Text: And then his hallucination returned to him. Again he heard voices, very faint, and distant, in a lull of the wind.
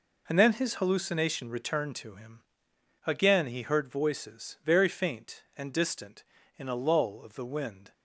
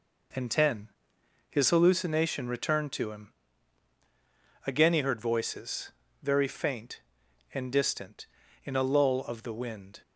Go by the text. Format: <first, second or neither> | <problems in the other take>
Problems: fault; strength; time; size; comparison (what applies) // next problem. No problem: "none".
first | says "ten" for "then"; at 0.4 s